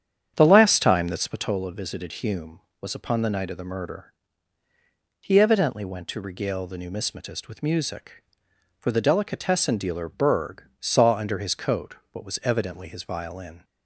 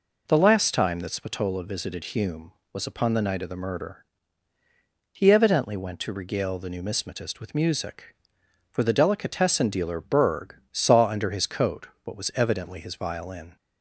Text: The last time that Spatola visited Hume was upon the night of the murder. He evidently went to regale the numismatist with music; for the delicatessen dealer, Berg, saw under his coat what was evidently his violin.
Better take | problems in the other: second | starts louder than the rest; strong; until 1.6 s; 9 dB // pauses between "coat" and "what"; slight; at 11.9 s; 0.18 s long; slight in the second

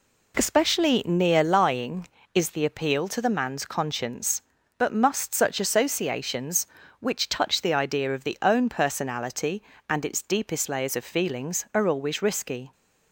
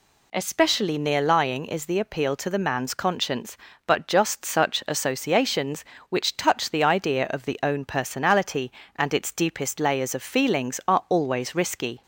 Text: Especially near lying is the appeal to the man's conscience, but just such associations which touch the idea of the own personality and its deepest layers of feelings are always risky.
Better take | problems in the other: second | says "must" for "just"; at 4.9 s

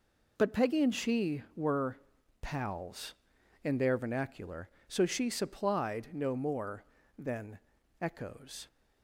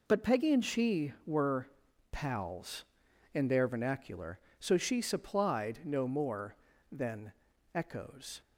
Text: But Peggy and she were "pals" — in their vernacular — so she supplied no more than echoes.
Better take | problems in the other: neither | pauses between "were" and "pals"; noticeable; the same in both // pauses between "than" and "echoes"; the same in both

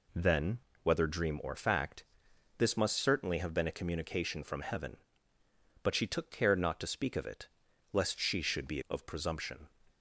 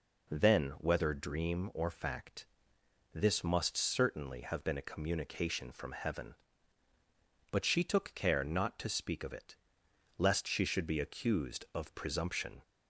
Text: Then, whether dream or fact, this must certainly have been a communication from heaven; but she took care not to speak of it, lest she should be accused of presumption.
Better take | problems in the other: second | skips "accused"; at 8.8 s

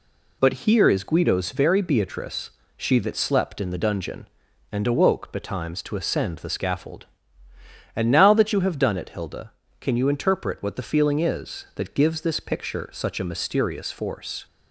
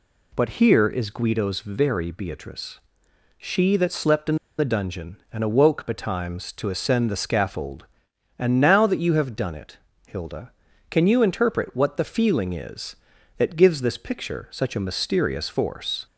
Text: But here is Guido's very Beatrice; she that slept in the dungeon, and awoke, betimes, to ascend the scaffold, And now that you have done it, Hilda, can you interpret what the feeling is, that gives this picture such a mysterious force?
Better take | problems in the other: first | pauses between "in" and "the"; slight; at 4.3 s; 0.23 s long

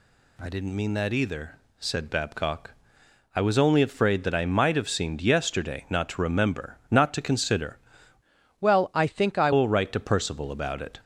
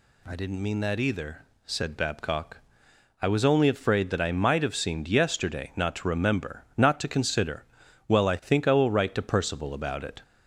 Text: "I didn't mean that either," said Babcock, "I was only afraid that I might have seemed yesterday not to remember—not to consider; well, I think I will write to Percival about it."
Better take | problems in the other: second | changes voice from "well" to "I"; from 8.6 to 9.5 s; 0.9 s long

